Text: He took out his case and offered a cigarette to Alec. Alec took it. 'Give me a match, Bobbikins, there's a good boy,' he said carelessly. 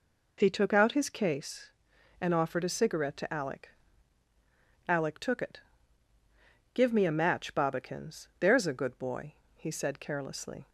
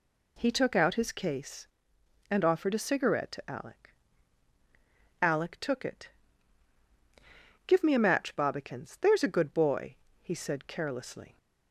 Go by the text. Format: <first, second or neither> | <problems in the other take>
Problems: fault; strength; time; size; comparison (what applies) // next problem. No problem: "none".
neither | none